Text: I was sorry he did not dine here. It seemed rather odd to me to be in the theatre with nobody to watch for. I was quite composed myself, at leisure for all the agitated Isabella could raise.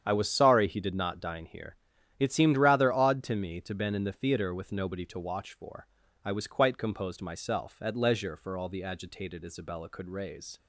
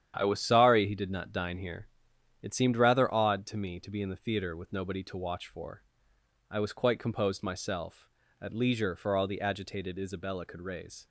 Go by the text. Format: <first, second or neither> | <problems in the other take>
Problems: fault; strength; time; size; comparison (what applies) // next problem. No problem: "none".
second | starts louder than the rest; strong; until 1.0 s; 8.5 dB; strong in the second // says "been" for "be"; at 3.7 s